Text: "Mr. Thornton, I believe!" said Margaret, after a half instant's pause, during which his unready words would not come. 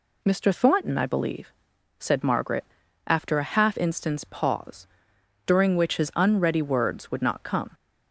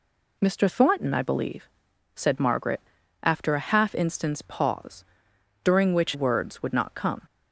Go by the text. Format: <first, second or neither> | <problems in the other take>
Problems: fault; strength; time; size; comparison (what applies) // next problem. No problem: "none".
first | skips "his unready"; at 6.1 s